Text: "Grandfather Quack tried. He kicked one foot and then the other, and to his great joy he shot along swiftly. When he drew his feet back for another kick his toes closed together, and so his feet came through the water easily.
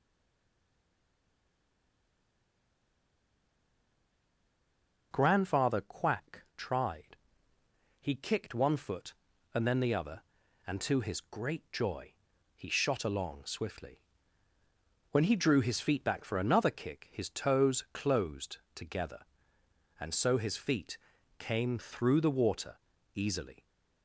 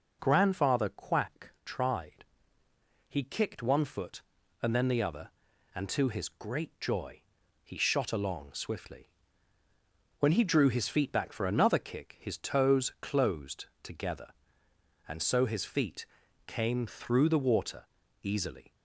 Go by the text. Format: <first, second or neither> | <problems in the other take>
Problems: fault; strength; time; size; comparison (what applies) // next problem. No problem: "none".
second | stays silent before the first word; strong; until 5.1 s; 5.1 s long // pauses between "joy" and "he"; at 12.1 s; 0.42 s long; also in the second // pauses between "closed" and "together"; slight; at 18.5 s; 0.18 s long; slight in the second // pauses between "feet" and "came"; at 20.9 s; 0.42 s long; also in the second // pauses between "water" and "easily"; slight; at 22.7 s; 0.36 s long; slight in the second